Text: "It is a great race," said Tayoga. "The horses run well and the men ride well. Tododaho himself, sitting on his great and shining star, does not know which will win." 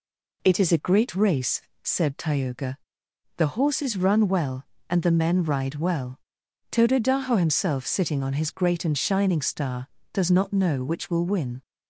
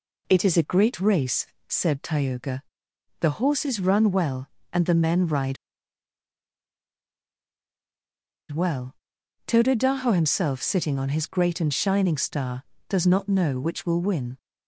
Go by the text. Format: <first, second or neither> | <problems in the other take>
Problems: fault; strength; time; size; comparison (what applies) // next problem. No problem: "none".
first | pauses between "ride" and "well"; strong; at 5.5 s; 2.9 s long